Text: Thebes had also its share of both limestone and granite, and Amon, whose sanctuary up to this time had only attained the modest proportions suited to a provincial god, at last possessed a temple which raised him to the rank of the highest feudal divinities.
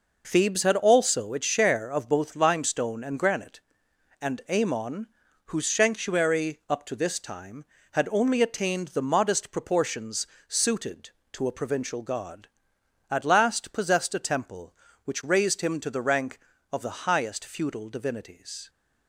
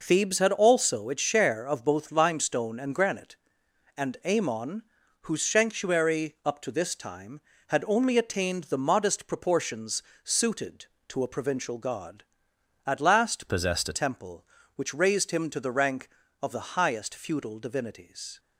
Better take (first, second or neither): first